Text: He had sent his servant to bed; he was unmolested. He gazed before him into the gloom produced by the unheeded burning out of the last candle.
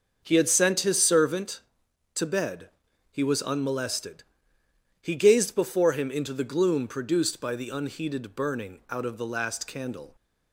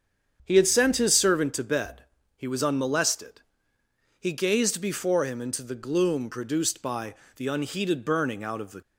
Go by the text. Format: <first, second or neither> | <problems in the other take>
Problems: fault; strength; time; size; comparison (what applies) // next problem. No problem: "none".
first | starts louder than the rest; strong; until 1.4 s; 7.5 dB; also in the first // pauses between "by" and "the"; slight; at 7.1 s; 0.24 s long // stops before "last candle"; at 8.8 s